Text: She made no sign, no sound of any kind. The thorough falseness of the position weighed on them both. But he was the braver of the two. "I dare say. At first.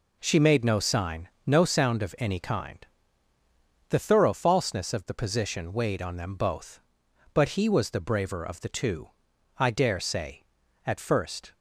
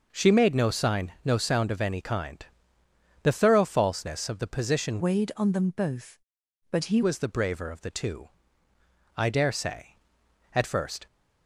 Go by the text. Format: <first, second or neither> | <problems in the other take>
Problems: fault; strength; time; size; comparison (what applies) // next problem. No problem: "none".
first | changes voice from "weighed" to "he"; from 4.9 to 7.0 s; 2.1 s long